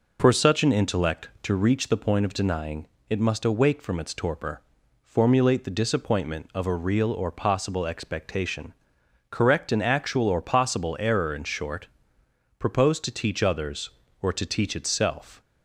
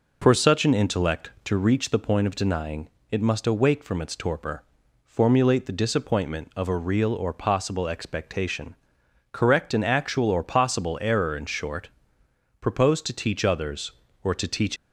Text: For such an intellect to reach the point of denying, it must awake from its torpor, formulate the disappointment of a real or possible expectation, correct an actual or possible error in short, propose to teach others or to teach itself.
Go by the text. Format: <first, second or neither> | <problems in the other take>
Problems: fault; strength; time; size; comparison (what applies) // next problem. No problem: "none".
first | stops before "itself"; at 14.7 s